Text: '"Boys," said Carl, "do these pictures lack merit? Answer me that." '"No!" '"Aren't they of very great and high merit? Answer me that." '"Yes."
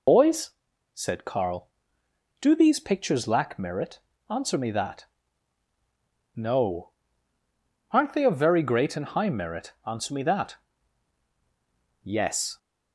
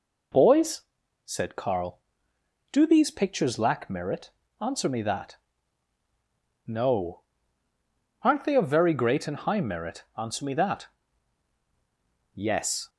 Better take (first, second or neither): second